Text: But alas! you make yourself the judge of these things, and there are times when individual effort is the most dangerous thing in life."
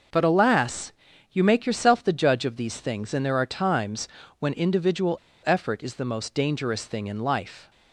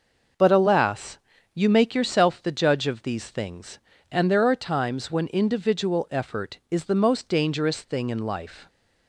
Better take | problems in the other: second | starts louder than the rest; until 1.5 s; 6 dB // pauses between "times" and "when"; slight; at 4.0 s; 0.32 s long // pauses between "individual" and "effort"; slight; at 5.1 s; 0.26 s long

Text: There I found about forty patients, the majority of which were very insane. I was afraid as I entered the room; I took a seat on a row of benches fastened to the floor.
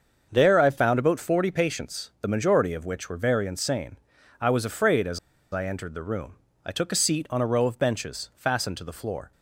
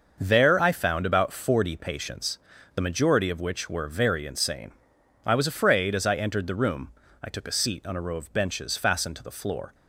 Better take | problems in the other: second | starts louder than the rest; until 1.3 s; 6.5 dB; also in the second // pauses between "as" and "I"; slight; at 5.1 s; 0.33 s long

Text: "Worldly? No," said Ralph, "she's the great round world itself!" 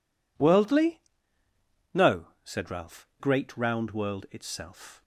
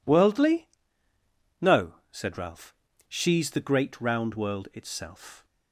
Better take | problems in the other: second | skips "she's the"; at 3.1 s

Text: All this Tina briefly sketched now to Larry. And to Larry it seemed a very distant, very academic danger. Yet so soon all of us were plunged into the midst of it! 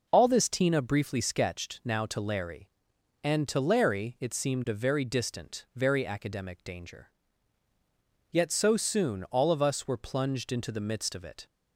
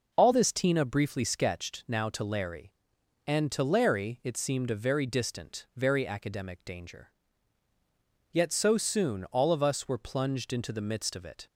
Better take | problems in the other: neither | none

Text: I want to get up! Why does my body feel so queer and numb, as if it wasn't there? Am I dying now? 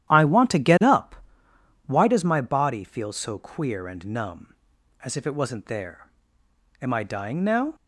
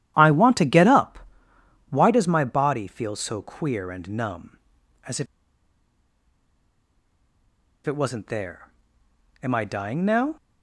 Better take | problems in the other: first | starts louder than the rest; strong; until 1.1 s; 11.5 dB; strong in the first // pauses between "if" and "it"; strong; at 5.2 s; 2.5 s long

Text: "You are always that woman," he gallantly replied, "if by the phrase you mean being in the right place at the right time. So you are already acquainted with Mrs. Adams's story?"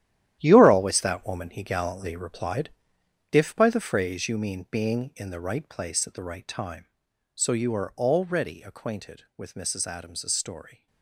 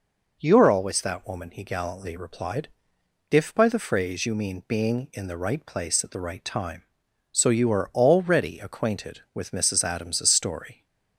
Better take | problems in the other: second | gets quieter; strong; throughout; 11 dB

